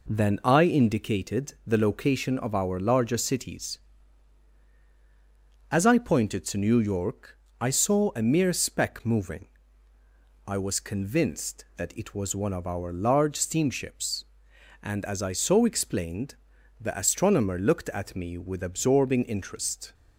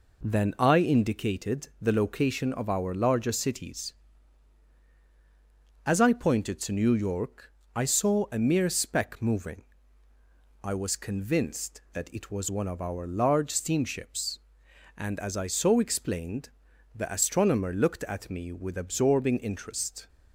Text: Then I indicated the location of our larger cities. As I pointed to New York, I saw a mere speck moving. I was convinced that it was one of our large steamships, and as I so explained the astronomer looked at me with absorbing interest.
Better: neither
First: pauses between "explained" and "the"; at 16.3 s; 0.44 s long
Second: pauses between "explained" and "the"; at 16.4 s; 0.44 s long

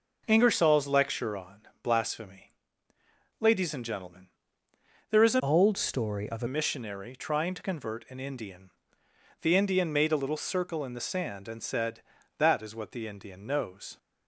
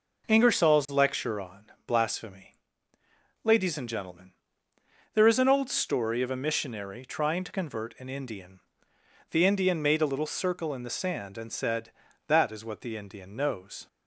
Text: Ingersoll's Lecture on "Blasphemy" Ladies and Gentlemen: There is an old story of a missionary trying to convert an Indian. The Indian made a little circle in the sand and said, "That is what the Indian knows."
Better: second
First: pauses between "on" and "Blasphemy"; slight; at 1.6 s; 0.20 s long // pauses between "Blasphemy" and "Ladies"; noticeable; at 2.5 s; 0.90 s long // changes voice from "old" to "a"; from 5.3 to 6.4 s; 1.1 s long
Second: pauses between "on" and "Blasphemy"; slight; at 1.6 s; 0.20 s long // pauses between "Blasphemy" and "Ladies"; noticeable; at 2.5 s; 0.90 s long

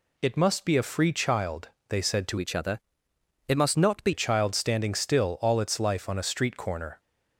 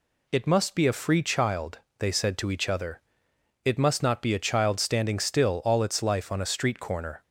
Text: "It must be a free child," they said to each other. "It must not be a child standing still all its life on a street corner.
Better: second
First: changes voice from "each" to "be"; from 2.3 to 4.1 s; 1.8 s long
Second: none

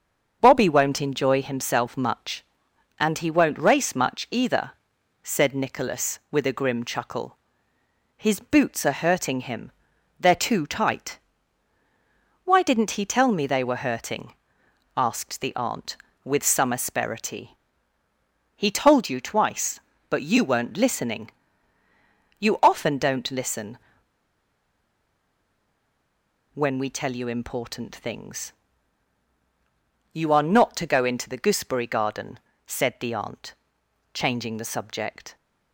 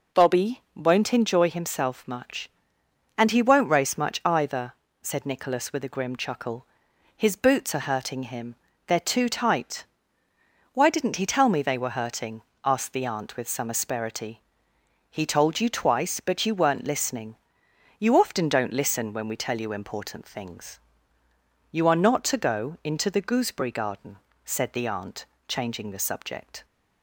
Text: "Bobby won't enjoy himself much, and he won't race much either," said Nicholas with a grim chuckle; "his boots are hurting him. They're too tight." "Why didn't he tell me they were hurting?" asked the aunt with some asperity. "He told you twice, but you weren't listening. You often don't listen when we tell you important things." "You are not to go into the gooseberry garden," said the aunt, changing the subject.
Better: second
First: starts louder than the rest; until 1.4 s; 6.5 dB // pauses between "listen" and "when"; strong; at 23.7 s; 2.7 s long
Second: none

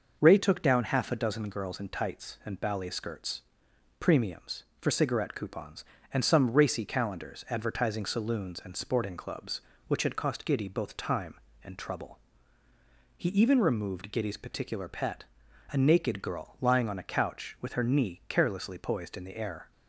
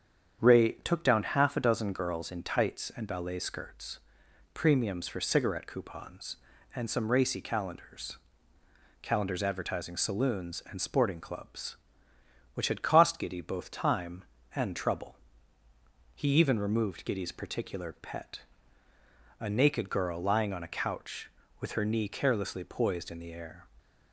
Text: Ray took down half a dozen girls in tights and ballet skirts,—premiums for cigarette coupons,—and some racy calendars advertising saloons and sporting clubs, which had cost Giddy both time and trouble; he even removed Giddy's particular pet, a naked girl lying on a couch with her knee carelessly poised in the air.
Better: first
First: none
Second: starts louder than the rest; strong; until 1.5 s; 8 dB // says "calendars" twice; at 9.0 s

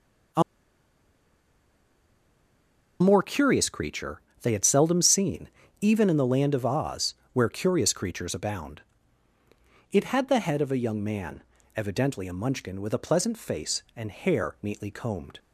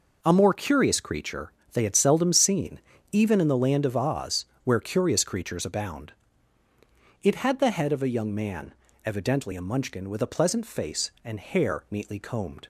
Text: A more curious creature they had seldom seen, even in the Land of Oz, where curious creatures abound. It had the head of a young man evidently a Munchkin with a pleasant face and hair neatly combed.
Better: second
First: pauses between "A" and "more"; strong; at 0.4 s; 2.5 s long // pauses between "creature" and "they"; slight; at 4.2 s; 0.22 s long // pauses between "man" and "evidently"; slight; at 11.4 s; 0.34 s long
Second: pauses between "creature" and "they"; slight; at 1.5 s; 0.22 s long // pauses between "man" and "evidently"; slight; at 8.7 s; 0.32 s long

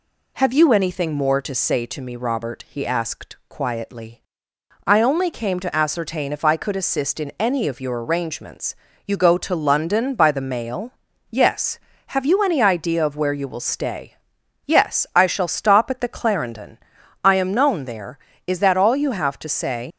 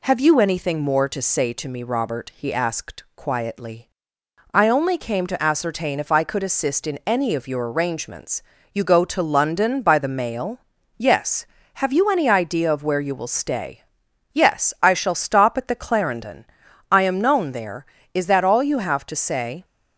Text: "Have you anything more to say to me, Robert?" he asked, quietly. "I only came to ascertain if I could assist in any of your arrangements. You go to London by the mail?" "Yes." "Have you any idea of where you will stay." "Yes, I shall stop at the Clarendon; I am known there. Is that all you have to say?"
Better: second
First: leaves "say" unfinished; at 19.9 s; 65 ms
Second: none

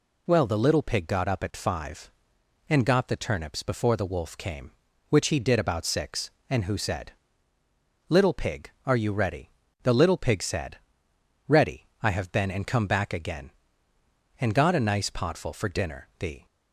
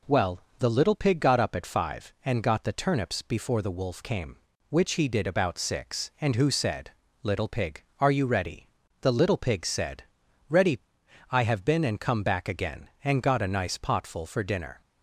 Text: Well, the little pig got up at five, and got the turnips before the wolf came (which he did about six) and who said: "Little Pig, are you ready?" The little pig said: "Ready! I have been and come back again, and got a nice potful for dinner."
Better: second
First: goes on to say "The"; slight; from 16.1 s on; 0.28 s long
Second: none

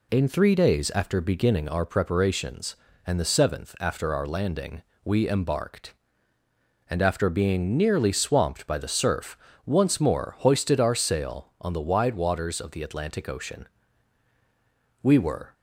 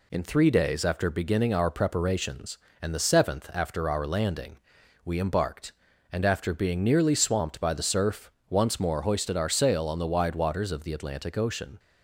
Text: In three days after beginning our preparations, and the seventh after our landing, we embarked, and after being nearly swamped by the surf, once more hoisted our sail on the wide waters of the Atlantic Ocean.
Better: second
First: goes on to say "We were"; from 15.0 s on; 0.50 s long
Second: none

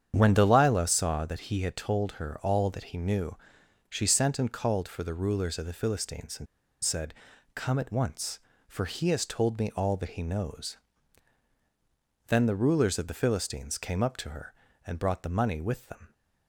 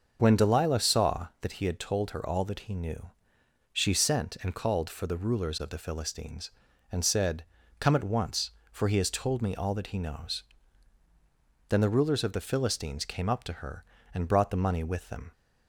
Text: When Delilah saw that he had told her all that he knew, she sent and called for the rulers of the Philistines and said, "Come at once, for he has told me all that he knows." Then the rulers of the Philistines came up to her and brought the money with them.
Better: second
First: starts louder than the rest; strong; until 1.1 s; 8.5 dB // pauses between "and" and "said"; at 6.4 s; 0.37 s long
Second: starts louder than the rest; until 1.2 s; 7 dB

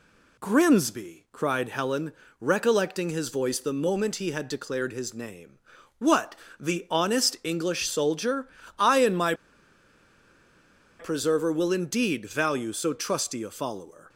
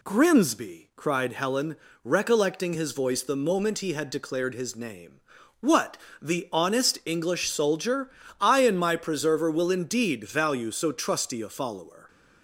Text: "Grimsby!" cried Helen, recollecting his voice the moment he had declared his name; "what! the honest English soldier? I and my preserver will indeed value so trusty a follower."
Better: second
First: pauses between "my" and "preserver"; strong; at 9.3 s; 1.6 s long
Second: none

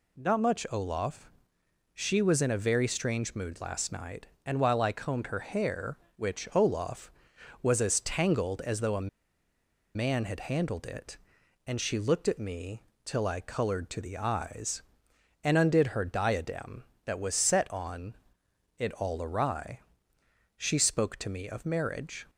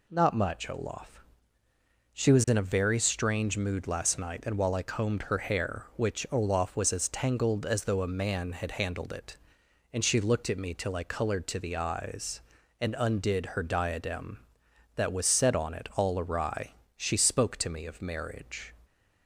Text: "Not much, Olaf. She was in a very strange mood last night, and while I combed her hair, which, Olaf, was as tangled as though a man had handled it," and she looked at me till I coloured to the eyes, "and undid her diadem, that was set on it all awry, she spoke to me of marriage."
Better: second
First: pauses between "a" and "man"; noticeable; at 9.0 s; 0.87 s long // pauses between "me" and "till"; slight; at 12.8 s; 0.22 s long // pauses between "on" and "it"; noticeable; at 18.1 s; 0.60 s long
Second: none

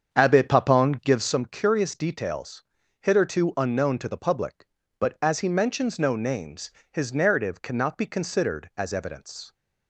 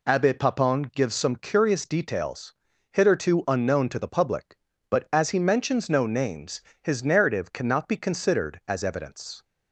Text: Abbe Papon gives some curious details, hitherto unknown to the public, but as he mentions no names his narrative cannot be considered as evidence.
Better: second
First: starts louder than the rest; strong; until 1.4 s; 7.5 dB // pauses between "names" and "his"; slight; at 6.6 s; 0.22 s long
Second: pauses between "names" and "his"; slight; at 6.5 s; 0.22 s long

